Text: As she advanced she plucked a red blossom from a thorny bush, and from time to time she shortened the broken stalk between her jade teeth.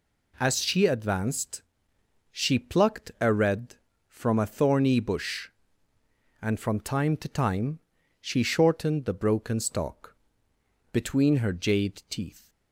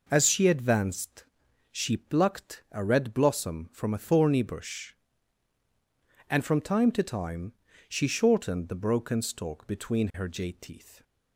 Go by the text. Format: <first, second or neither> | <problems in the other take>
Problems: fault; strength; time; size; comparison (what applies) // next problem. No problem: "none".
second | pauses between "advanced" and "she"; noticeable; at 1.6 s; 0.68 s long; noticeable in the second // skips "blossom"; at 3.9 s // pauses between "time" and "she"; at 7.7 s; 0.40 s long; slight in the second // pauses between "stalk" and "between"; noticeable; at 10.1 s; 0.76 s long